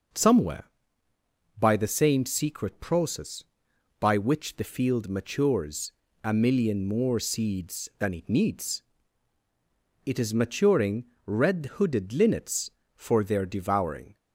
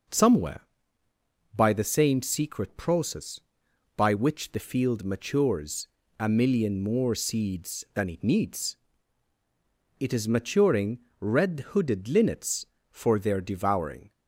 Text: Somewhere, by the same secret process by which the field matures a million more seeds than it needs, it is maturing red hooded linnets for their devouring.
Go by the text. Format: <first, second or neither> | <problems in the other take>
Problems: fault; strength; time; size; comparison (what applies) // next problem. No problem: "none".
neither | pauses between "matures" and "a"; slight; the same in both // pauses between "maturing" and "red"; slight; the same in both